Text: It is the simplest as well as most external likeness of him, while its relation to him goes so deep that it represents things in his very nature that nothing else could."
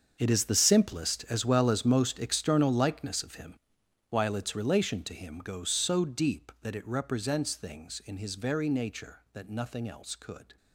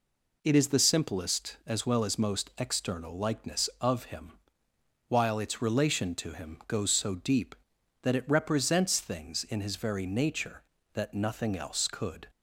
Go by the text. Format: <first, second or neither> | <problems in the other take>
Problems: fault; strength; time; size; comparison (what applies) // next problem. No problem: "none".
second | gets quieter; strong; throughout; 14.5 dB